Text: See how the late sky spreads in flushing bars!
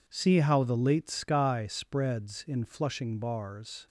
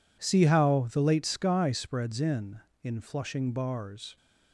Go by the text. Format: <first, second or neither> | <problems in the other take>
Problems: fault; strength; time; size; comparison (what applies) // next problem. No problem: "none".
first | says "in" twice; at 2.8 s